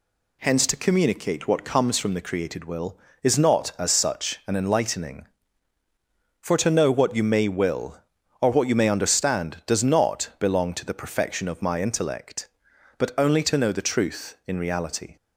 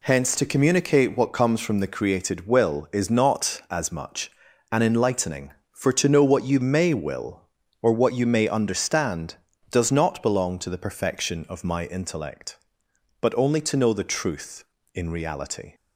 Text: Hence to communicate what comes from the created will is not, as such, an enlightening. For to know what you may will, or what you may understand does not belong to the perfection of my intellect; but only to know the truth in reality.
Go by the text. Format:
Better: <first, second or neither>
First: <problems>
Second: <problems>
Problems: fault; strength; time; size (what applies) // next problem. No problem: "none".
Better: first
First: none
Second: says "much" for "such"; at 3.9 s